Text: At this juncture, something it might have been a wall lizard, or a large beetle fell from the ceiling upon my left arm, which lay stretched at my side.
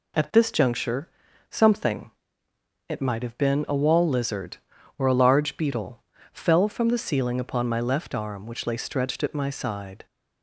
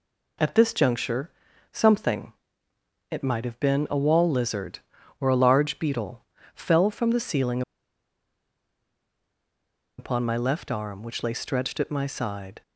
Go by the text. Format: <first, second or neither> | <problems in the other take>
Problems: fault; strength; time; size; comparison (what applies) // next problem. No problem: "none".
first | pauses between "something" and "it"; noticeable; at 2.3 s; 0.80 s long; noticeable in the first // pauses between "beetle" and "fell"; slight; at 6.2 s; 0.32 s long; slight in the first // pauses between "ceiling" and "upon"; strong; at 7.6 s; 2.3 s long